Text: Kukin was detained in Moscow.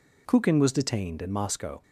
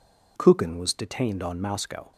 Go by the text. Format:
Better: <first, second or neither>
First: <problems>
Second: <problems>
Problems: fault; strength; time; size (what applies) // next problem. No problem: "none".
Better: first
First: none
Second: says "on" for "in"; at 1.4 s